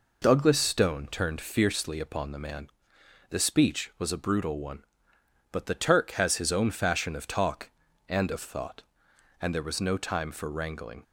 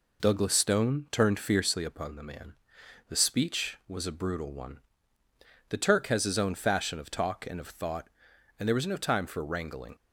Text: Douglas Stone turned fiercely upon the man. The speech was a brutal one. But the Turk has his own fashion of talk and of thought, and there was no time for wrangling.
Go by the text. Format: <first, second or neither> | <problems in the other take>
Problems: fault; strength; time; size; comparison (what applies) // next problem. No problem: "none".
first | skips "But"; at 5.2 s